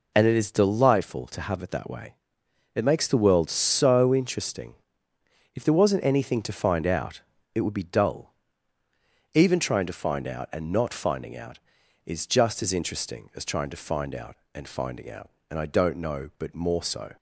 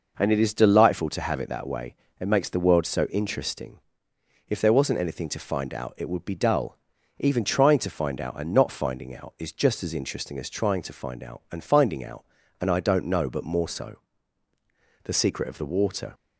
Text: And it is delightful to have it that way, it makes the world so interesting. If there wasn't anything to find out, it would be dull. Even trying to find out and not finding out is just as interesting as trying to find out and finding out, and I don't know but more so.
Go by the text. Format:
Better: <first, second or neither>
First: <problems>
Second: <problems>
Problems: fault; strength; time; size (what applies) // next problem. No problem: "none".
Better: first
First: none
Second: goes on to say "The secret of the water"; noticeable; from 15.0 s on; 1.1 s long